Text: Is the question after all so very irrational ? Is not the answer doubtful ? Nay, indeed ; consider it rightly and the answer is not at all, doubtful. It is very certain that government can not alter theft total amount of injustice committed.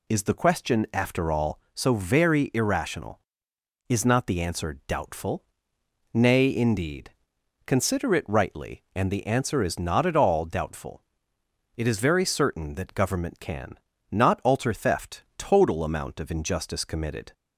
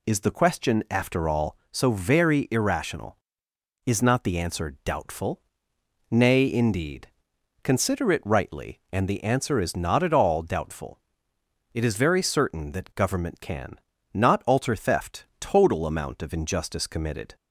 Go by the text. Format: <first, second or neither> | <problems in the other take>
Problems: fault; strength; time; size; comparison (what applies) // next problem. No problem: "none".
neither | pauses between "can" and "not"; slight; the same in both